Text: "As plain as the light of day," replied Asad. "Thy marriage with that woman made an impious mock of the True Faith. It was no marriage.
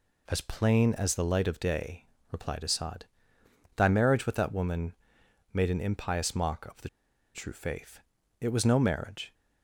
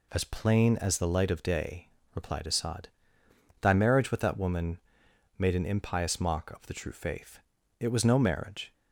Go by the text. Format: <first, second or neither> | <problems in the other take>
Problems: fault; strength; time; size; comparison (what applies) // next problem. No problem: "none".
second | pauses between "woman" and "made"; noticeable; at 4.9 s; 0.58 s long; noticeable in the second // pauses between "the" and "True"; noticeable; at 6.8 s; 0.47 s long